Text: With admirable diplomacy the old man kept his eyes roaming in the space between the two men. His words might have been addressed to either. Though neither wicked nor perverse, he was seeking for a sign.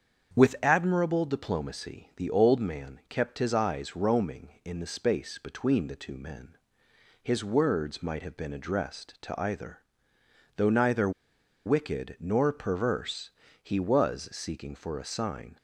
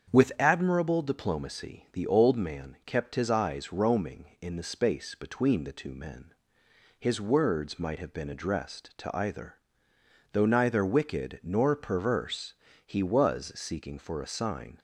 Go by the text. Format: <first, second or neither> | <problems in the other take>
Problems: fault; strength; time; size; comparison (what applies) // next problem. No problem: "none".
second | starts louder than the rest; strong; until 1.3 s; 7.5 dB; strong in the second // pauses between "neither" and "wicked"; noticeable; at 11.0 s; 0.57 s long